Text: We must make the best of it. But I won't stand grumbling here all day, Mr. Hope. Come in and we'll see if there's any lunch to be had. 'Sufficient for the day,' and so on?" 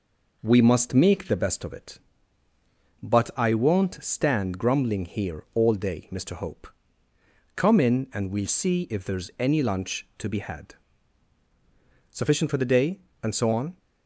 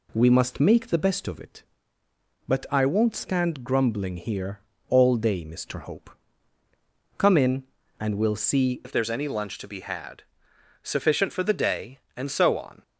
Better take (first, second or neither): first